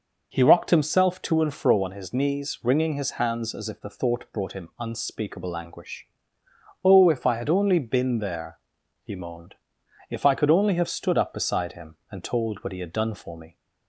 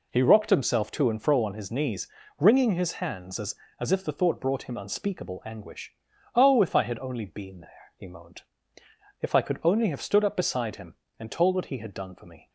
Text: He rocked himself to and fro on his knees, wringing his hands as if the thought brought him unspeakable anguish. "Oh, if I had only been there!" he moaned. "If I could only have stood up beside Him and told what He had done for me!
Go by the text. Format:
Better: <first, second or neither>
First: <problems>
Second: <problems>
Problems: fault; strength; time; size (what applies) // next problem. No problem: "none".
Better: first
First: none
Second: says "as" twice; at 3.7 s